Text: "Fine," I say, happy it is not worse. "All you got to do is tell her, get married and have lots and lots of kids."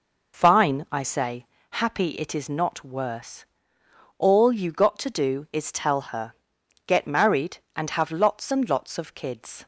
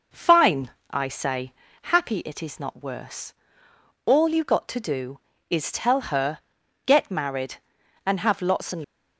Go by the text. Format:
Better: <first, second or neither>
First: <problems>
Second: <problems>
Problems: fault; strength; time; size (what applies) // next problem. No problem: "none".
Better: first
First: none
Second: stops before "lots of kids"; at 8.8 s